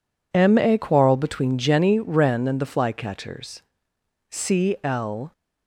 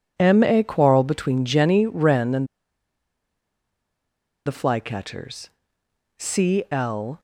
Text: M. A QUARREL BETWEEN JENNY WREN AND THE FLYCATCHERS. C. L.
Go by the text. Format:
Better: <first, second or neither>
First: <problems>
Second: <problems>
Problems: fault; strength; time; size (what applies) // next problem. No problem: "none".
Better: first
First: none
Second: pauses between "AND" and "THE"; strong; at 2.4 s; 2.0 s long